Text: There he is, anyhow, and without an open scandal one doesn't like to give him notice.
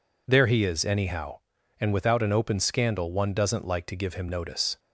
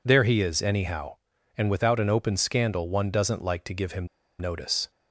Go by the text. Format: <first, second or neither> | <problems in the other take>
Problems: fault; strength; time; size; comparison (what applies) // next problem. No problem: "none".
first | pauses between "him" and "notice"; slight; at 4.0 s; 0.32 s long